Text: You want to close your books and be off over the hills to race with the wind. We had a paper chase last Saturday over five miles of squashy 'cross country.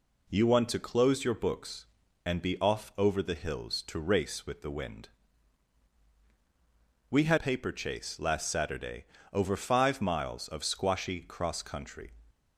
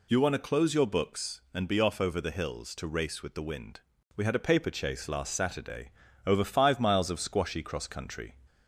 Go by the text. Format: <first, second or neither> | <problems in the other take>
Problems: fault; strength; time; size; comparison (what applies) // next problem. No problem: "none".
second | skips "a"; at 7.3 s // pauses between "Saturday" and "over"; slight; at 9.0 s; 0.26 s long; slight in the second